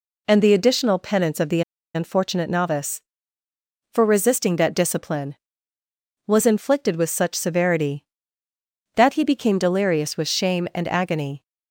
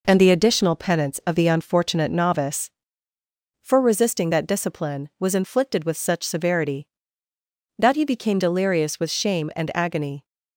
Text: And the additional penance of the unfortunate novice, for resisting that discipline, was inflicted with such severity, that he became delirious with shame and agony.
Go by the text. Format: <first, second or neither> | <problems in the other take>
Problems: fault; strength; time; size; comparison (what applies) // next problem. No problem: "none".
second | pauses between "the" and "unfortunate"; slight; at 1.6 s; 0.33 s long